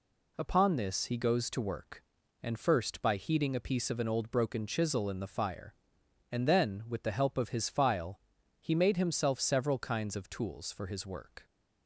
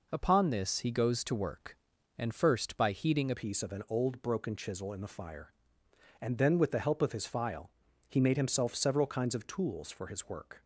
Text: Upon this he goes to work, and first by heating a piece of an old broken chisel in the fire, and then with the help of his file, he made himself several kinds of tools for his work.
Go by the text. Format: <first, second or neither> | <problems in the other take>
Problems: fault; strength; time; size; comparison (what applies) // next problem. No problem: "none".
first | changes voice at "piece"; from 3.3 s on; 7.3 s long